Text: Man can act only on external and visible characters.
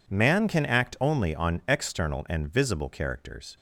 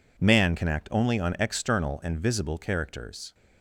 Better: neither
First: none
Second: none

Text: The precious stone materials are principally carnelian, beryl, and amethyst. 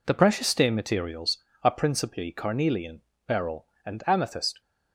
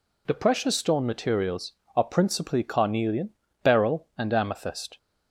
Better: second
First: says "stain" for "stone"; at 0.4 s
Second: none

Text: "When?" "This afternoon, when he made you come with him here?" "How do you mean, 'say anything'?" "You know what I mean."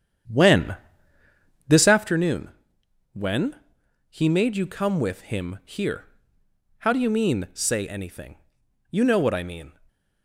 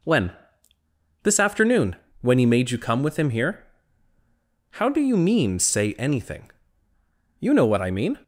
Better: second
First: starts louder than the rest; strong; until 2.1 s; 8.5 dB // pauses between "when" and "he"; noticeable; at 3.5 s; 0.54 s long // stays silent after the last word; slight; from 9.7 s on; 0.5 s long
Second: none

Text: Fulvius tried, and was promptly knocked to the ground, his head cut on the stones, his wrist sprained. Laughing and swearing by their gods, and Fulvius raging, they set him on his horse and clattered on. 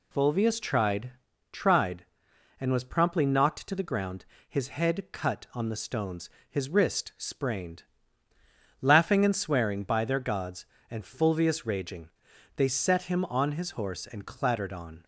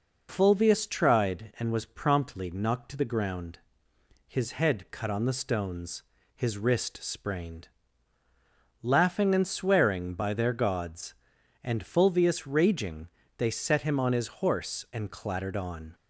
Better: second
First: says "tried" twice; at 1.5 s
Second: none

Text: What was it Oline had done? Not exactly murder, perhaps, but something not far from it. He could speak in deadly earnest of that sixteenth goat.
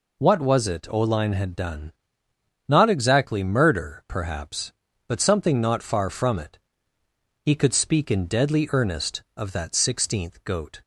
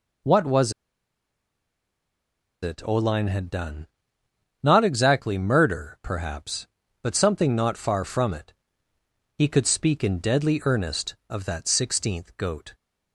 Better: first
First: none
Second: pauses between "was" and "it"; strong; at 0.7 s; 1.9 s long

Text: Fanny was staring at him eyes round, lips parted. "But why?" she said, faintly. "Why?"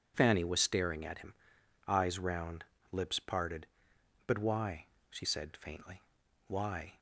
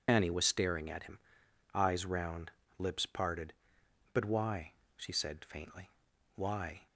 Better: first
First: pauses between "him" and "eyes"; noticeable; at 1.3 s; 0.54 s long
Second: loses the start of "Fanny"; at 0.0 s; 80 ms // pauses between "him" and "eyes"; noticeable; at 1.1 s; 0.56 s long

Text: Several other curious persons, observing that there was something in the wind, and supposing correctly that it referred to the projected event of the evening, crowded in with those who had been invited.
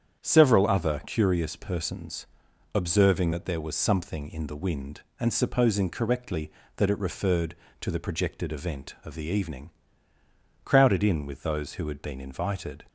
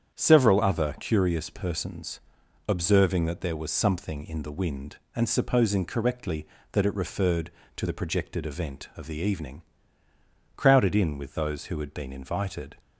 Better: neither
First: starts louder than the rest; strong; until 1.2 s; 8.5 dB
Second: starts louder than the rest; strong; until 1.2 s; 8.5 dB

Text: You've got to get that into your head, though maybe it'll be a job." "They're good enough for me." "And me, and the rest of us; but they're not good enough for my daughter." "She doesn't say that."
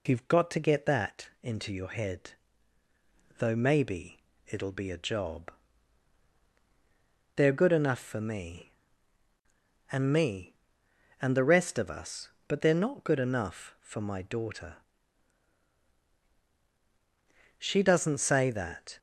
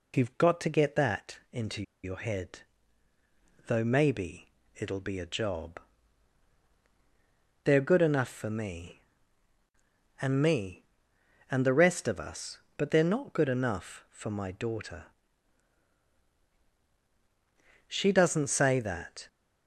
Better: first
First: pauses between "maybe" and "it'll"; slight; at 4.1 s; 0.28 s long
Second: pauses between "into" and "your"; slight; at 1.8 s; 0.20 s long // pauses between "maybe" and "it'll"; slight; at 4.4 s; 0.28 s long

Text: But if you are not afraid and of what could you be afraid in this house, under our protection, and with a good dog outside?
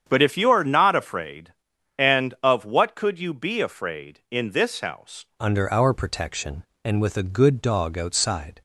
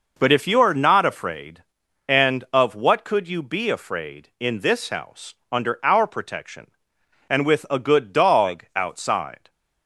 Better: second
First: starts louder than the rest; strong; until 1.0 s; 8 dB // changes voice at "under"; from 5.3 s on; 3.3 s long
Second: none

